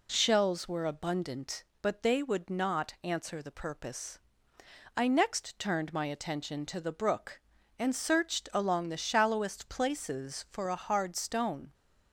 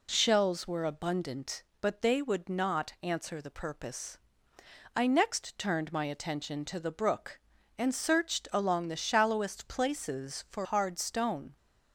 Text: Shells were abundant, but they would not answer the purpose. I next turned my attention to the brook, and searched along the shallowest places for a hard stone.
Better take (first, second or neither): first